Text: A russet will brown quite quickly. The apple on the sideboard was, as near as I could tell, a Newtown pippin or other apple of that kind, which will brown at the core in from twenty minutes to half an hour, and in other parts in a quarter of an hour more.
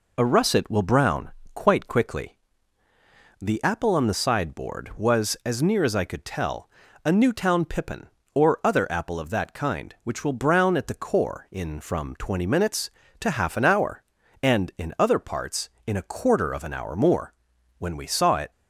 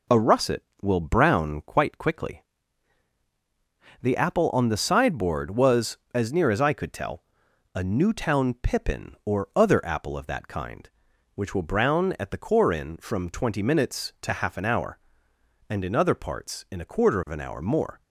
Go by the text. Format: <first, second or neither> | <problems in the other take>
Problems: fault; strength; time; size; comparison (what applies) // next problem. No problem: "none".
second | pauses between "brown" and "quite"; slight; at 1.3 s; 0.22 s long // goes on to say "When we saw it"; noticeable; from 17.7 s on; 0.74 s long